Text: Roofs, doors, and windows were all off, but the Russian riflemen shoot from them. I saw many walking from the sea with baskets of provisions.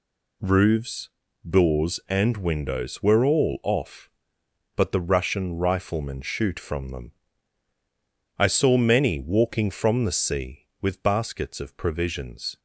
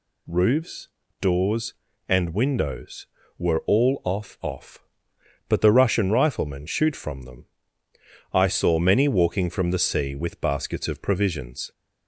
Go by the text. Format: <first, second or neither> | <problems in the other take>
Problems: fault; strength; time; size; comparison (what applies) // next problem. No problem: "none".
first | says "off" twice; at 4.4 s